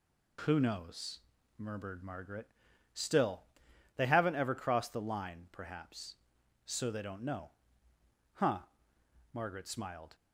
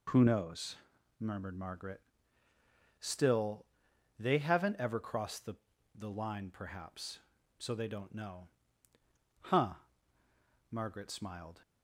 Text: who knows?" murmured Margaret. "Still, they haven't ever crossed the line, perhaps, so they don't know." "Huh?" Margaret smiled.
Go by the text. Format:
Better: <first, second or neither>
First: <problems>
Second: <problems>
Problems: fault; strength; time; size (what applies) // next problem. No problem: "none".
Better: first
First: none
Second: says "the" twice; at 5.9 s